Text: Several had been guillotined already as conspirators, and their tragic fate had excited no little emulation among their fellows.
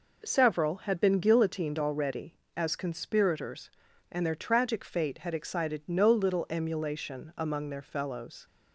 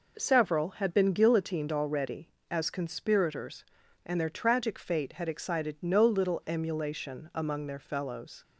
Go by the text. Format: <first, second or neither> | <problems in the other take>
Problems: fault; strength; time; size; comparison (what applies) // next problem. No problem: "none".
neither | none